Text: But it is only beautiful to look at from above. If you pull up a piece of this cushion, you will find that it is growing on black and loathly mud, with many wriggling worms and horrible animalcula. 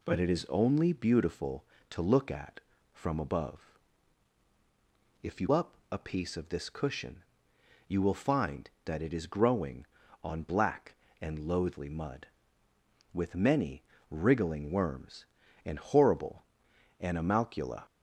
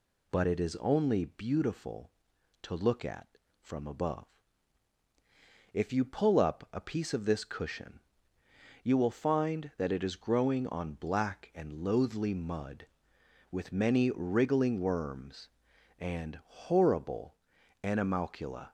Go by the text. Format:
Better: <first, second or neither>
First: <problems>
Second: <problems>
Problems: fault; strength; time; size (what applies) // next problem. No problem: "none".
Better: second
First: skips "pull"; at 5.4 s // pauses between "up" and "a"; slight; at 5.7 s; 0.16 s long // pauses between "many" and "wriggling"; slight; at 13.8 s; 0.26 s long // pauses between "horrible" and "animalcula"; noticeable; at 16.4 s; 0.56 s long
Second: pauses between "horrible" and "animalcula"; noticeable; at 17.3 s; 0.46 s long